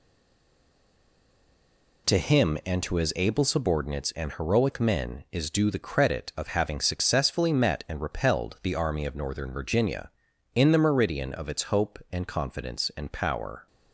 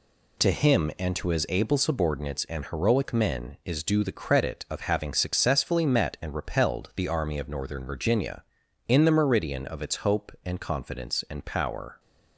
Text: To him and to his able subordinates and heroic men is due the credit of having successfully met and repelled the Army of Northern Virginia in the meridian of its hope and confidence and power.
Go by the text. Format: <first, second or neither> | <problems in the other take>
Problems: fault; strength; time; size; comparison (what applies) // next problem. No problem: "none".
second | stays silent before the first word; noticeable; until 2.0 s; 2.0 s long